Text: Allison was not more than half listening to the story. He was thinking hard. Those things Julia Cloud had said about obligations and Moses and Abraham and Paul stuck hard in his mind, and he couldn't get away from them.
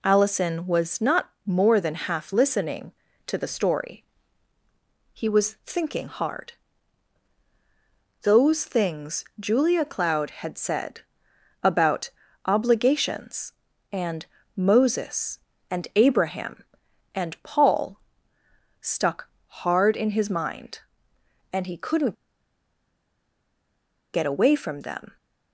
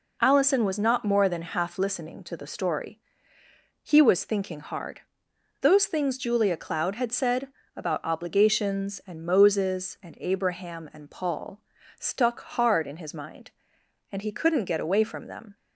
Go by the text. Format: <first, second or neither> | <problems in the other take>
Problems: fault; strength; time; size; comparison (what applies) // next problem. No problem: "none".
second | pauses between "not" and "more"; slight; at 1.2 s; 0.16 s long // pauses between "said" and "about"; noticeable; at 11.0 s; 0.62 s long; slight in the second // pauses between "about" and "obligations"; slight; at 12.1 s; 0.34 s long // pauses between "and" and "Moses"; slight; at 14.2 s; 0.30 s long // pauses between "Paul" and "stuck"; noticeable; at 17.9 s; 0.82 s long; also in the second // pauses between "stuck" and "hard"; slight; at 19.2 s; 0.20 s long // pauses between "couldn't" and "get"; strong; at 22.1 s; 1.9 s long